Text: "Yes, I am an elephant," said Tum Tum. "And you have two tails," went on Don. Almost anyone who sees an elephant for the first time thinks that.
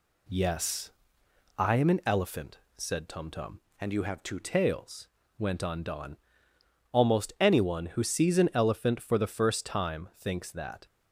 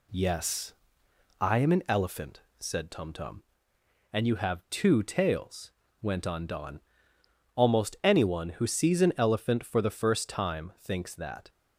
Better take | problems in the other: second | changes voice from "And" to "two"; from 3.7 to 4.4 s; 0.7 s long

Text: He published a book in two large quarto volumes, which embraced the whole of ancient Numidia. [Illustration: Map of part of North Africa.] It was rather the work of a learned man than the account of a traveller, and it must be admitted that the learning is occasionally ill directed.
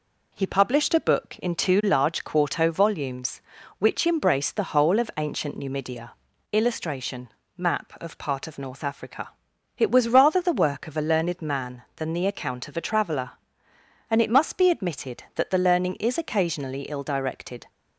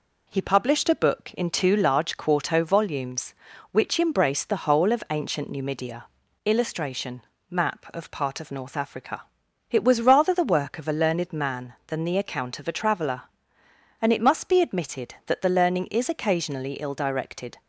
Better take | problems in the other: neither | none

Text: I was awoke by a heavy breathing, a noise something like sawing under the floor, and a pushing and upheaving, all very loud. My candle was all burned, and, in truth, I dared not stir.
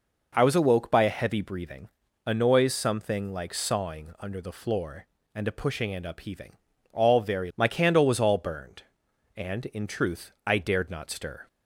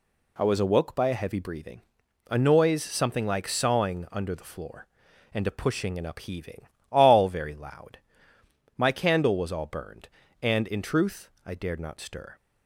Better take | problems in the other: second | skips "loud"; at 7.5 s

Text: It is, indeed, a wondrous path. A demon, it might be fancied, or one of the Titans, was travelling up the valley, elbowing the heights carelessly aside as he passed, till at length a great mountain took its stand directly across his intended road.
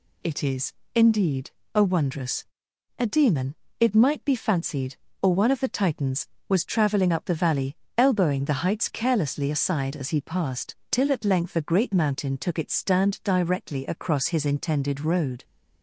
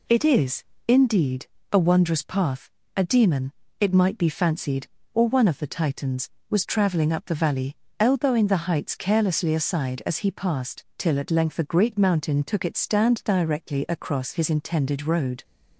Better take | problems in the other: second | skips "path"; at 2.7 s

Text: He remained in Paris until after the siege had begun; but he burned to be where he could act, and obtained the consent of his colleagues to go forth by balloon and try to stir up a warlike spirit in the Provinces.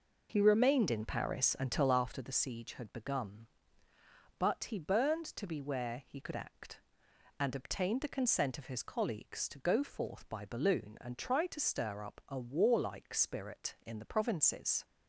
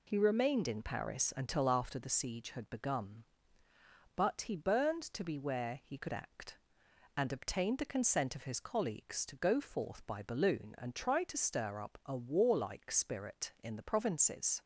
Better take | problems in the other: second | starts louder than the rest; noticeable; until 2.0 s; 5 dB

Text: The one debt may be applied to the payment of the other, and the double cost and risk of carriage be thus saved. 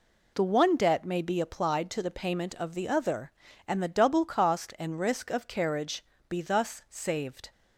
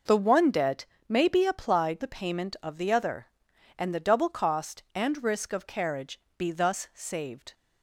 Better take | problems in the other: first | pauses between "debt" and "may"; slight; at 0.8 s; 0.24 s long // skips "to"; at 2.0 s // pauses between "carriage" and "be"; slight; at 6.1 s; 0.18 s long; slight in the first

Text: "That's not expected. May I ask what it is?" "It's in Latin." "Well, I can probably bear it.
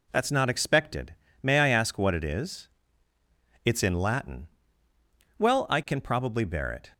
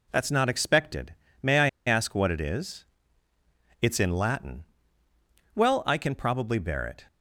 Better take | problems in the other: first | pauses between "I" and "ask"; slight; at 1.6 s; 0.19 s long

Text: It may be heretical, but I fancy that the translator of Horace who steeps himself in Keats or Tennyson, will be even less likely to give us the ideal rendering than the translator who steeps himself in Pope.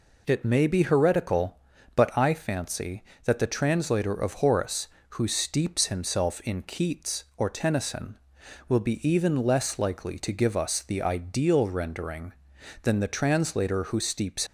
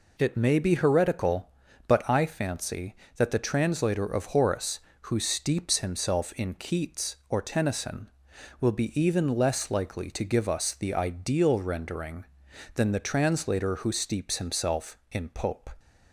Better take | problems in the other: second | stops before "himself in Pope"; at 14.4 s

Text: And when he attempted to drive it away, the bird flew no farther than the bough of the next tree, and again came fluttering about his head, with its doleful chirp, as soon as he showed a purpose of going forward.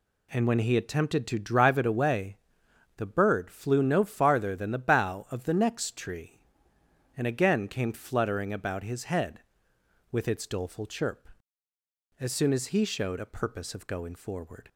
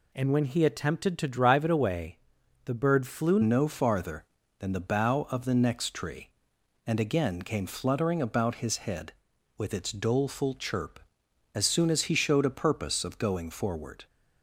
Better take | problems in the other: first | changes voice at "no"; from 3.4 s on; 10.6 s long

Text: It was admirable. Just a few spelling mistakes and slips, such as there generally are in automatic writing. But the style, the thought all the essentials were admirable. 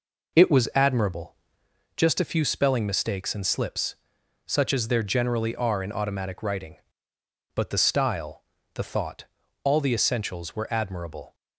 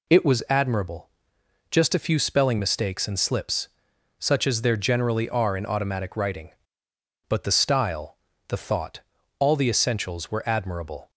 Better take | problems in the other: second | starts louder than the rest; noticeable; until 1.9 s; 4.5 dB // pauses between "thought" and "all"; at 9.2 s; 0.38 s long; also in the second

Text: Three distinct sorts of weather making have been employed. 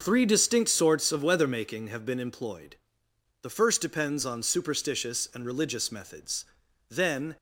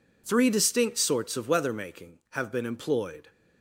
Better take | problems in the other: second | starts louder than the rest; noticeable; until 1.0 s; 6 dB // goes on to say "The first depends on superstitious and religious methods then"; strong; from 3.4 s on; 3.9 s long

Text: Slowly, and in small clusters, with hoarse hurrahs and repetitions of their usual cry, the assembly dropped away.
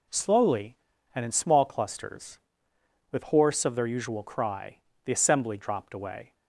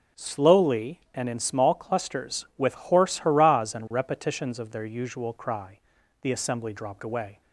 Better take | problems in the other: second | skips "hurrahs and repetitions"; at 3.6 s

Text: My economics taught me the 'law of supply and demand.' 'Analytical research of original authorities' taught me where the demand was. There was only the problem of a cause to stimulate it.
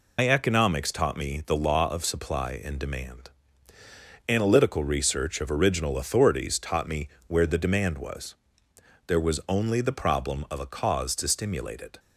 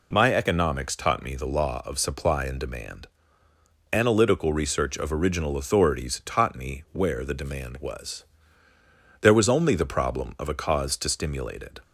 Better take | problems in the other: second | loses the start of "My"; at 0.1 s; 95 ms // pauses between "me" and "where"; slight; at 7.0 s; 0.18 s long

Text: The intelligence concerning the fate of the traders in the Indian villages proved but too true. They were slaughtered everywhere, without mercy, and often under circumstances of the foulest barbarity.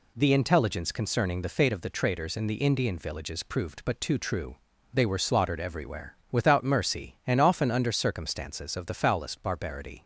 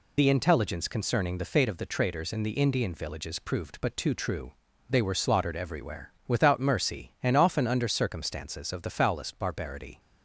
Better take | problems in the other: first | loses the start of "The"; at 0.1 s; 65 ms

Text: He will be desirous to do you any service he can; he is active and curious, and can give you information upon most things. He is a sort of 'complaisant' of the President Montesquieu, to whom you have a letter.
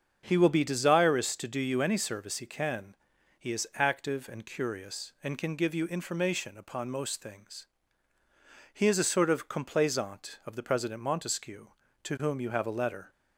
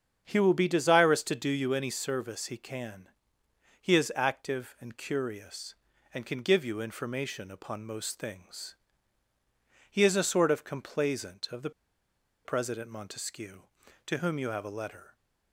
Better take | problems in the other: first | starts louder than the rest; strong; until 1.2 s; 7.5 dB; also in the first // pauses between "the" and "President"; noticeable; at 11.6 s; 0.75 s long

